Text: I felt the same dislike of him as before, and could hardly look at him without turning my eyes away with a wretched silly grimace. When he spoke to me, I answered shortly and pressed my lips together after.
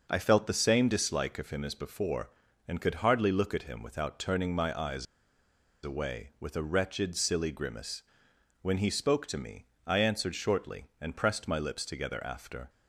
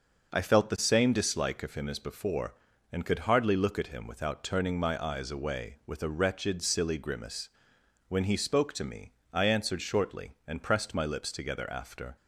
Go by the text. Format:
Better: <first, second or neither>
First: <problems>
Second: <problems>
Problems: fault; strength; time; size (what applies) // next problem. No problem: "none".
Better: second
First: pauses between "eyes" and "away"; noticeable; at 5.0 s; 0.78 s long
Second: none